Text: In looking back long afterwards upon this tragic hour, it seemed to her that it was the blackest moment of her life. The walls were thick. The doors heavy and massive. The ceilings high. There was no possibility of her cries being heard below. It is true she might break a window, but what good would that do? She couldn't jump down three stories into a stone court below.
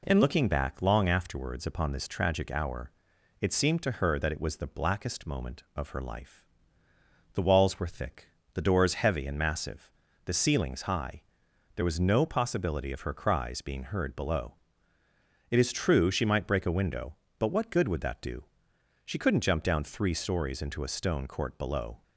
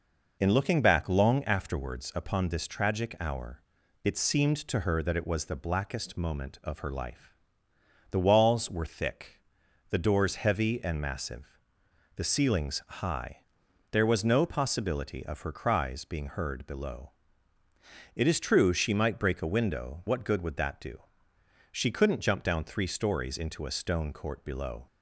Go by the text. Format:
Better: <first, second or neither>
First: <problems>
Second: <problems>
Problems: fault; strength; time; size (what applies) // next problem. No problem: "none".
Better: first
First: none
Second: skips "but"; at 20.0 s